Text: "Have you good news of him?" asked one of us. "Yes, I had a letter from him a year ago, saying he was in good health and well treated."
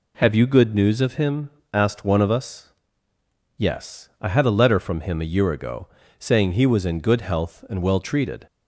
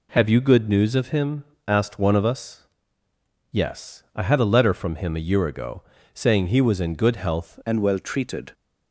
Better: first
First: none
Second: changes voice at "and"; from 7.6 s on; 0.9 s long

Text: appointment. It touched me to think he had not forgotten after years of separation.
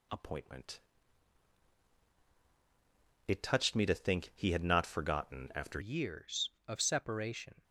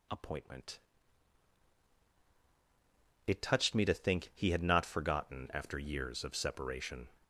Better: second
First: changes voice at "years"; from 5.8 s on; 1.8 s long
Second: none

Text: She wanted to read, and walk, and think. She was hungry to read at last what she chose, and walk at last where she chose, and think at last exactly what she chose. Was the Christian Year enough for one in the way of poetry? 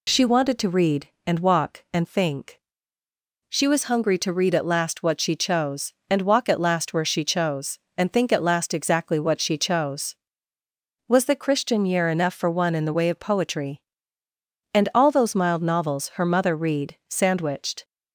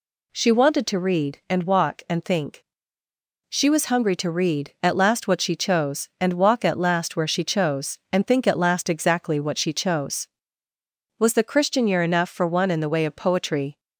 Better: second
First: goes on to say "And all those mild novels her mother read sandwiched"; strong; from 14.7 s on; 3.1 s long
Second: none

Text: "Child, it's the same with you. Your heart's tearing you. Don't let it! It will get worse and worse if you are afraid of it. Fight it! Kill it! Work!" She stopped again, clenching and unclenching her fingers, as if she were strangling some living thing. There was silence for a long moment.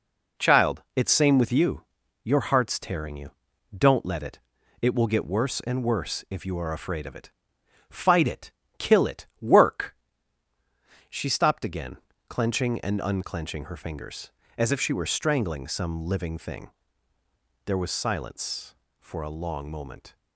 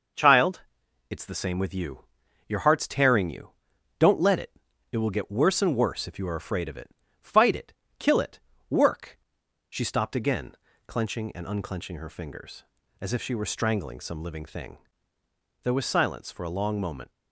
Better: second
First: skips "the"; at 1.1 s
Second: none

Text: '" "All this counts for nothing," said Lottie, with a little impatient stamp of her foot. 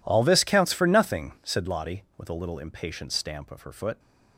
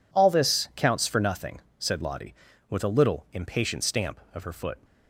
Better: neither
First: none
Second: none

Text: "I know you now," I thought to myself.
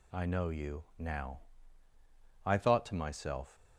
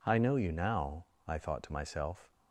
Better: neither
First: none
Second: none

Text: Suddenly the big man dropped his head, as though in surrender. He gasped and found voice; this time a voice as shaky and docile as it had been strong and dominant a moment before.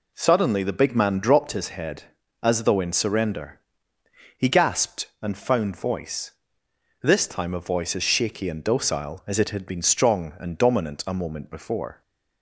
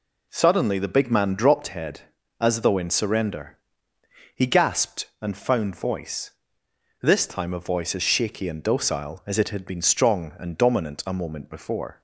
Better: first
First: none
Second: skips "his"; at 1.6 s

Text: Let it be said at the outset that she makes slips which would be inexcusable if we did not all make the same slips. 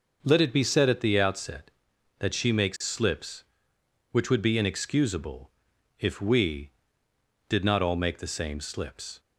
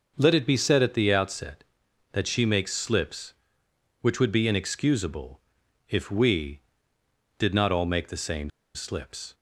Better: first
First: pauses between "inexcusable" and "if"; noticeable; at 5.4 s; 0.50 s long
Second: pauses between "inexcusable" and "if"; noticeable; at 5.3 s; 0.50 s long // pauses between "same" and "slips"; slight; at 8.4 s; 0.25 s long

